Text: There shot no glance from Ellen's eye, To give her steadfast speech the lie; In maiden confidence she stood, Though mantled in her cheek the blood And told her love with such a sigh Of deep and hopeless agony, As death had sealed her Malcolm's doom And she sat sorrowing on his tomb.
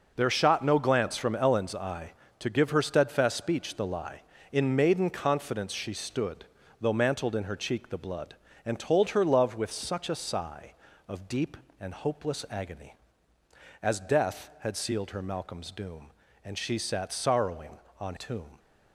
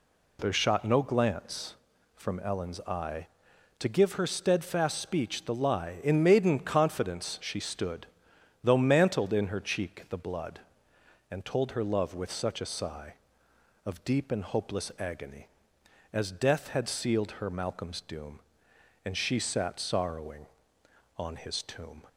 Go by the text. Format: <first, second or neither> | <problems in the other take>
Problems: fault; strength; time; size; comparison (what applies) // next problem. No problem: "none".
second | skips "his"; at 18.1 s